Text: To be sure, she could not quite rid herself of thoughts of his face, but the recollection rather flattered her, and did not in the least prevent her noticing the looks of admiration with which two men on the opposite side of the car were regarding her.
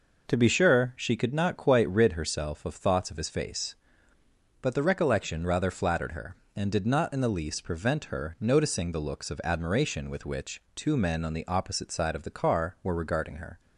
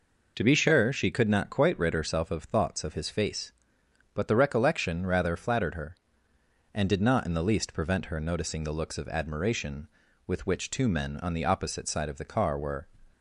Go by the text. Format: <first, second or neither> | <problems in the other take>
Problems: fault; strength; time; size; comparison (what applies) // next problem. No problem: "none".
first | stops before "regarding her"; at 13.1 s